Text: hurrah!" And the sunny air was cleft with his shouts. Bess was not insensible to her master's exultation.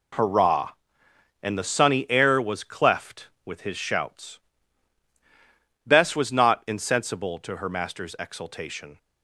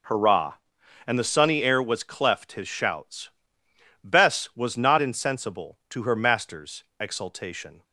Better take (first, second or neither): first